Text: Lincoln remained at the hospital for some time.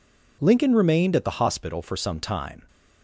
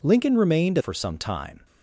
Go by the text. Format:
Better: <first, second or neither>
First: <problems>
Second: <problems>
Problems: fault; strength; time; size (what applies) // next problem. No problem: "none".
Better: first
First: none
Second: skips "at the hospital"; at 0.7 s